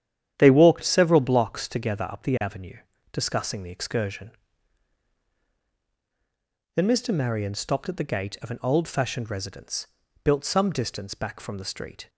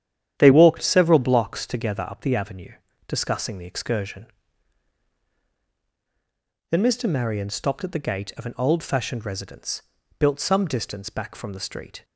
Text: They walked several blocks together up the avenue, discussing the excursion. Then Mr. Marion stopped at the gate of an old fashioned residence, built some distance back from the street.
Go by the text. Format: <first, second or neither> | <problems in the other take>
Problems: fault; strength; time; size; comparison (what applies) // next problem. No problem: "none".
neither | starts louder than the rest; strong; the same in both